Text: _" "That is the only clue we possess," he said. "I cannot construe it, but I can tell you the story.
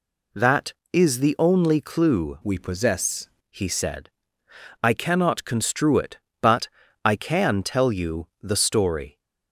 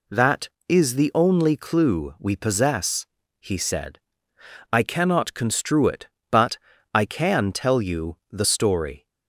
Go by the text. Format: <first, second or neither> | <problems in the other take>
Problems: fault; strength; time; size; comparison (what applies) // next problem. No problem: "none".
second | changes voice from "we" to "possess"; from 2.4 to 3.2 s; 0.8 s long // pauses between "but" and "I"; slight; at 6.6 s; 0.36 s long; slight in the second // pauses between "you" and "the"; slight; at 8.2 s; 0.16 s long; slight in the second